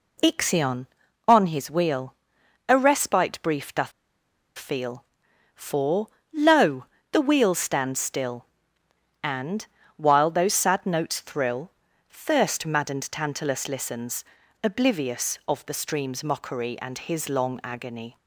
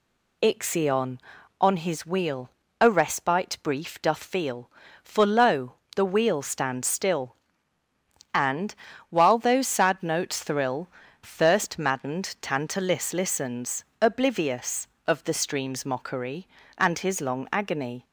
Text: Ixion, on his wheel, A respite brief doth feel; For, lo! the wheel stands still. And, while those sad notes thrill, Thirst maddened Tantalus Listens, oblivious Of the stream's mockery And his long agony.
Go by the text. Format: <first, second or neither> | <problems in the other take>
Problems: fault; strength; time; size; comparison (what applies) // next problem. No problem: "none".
second | pauses between "doth" and "feel"; noticeable; at 3.9 s; 0.67 s long